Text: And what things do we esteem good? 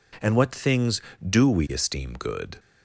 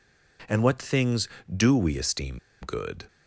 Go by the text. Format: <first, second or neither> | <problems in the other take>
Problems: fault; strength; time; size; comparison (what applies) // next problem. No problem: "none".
first | pauses between "esteem" and "good"; slight; at 2.3 s; 0.23 s long